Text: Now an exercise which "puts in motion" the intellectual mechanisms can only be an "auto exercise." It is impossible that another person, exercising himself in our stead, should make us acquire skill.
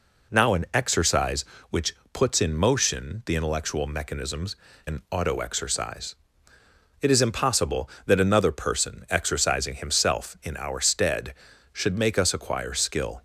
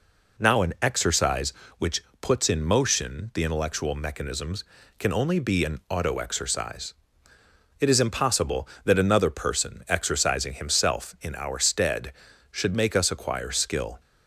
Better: second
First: pauses between "which" and "puts"; slight; at 1.9 s; 0.18 s long // skips "can only be"; at 4.7 s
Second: pauses between "which" and "puts"; slight; at 2.0 s; 0.18 s long

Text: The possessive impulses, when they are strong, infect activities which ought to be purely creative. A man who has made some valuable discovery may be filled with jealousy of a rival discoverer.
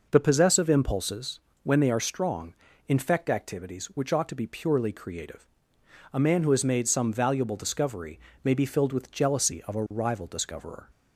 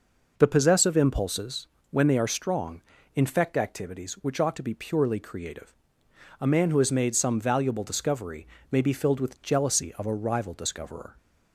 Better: neither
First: pauses between "discovery" and "may"; slight; at 8.1 s; 0.24 s long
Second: pauses between "discovery" and "may"; slight; at 8.4 s; 0.24 s long

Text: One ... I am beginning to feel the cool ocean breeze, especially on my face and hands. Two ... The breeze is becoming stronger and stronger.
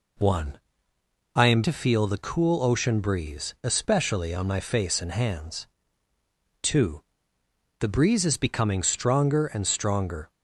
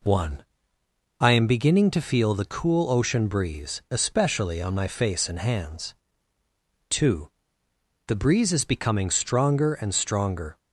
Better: second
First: skips "beginning"; at 1.6 s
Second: none

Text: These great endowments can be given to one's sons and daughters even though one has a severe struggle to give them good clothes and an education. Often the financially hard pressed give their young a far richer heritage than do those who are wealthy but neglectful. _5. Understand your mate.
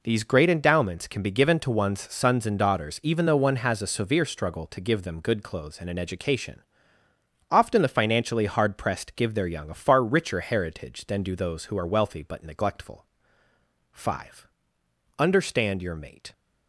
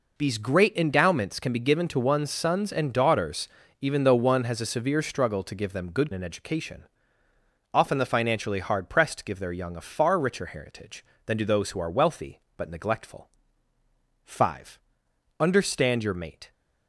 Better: first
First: none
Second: pauses between "daughters" and "even"; slight; at 3.4 s; 0.32 s long // skips "clothes and"; at 6.1 s

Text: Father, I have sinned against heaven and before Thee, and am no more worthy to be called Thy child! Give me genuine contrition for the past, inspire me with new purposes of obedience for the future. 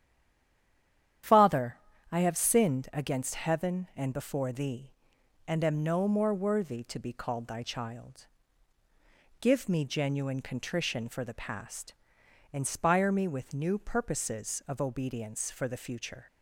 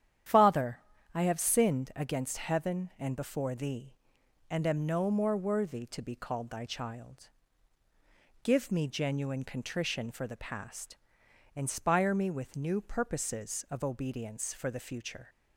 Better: second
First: stays silent before the first word; noticeable; until 1.2 s; 1.2 s long // starts louder than the rest; strong; until 2.6 s; 9.5 dB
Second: starts louder than the rest; strong; until 1.7 s; 9.5 dB

